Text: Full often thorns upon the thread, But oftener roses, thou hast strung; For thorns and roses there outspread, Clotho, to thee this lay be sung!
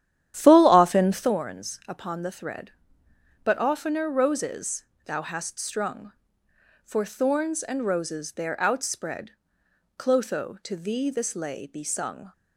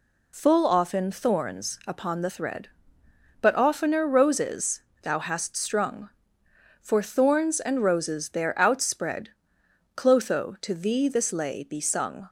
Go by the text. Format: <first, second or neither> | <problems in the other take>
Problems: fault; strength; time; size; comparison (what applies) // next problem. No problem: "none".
second | starts louder than the rest; strong; until 1.3 s; 11 dB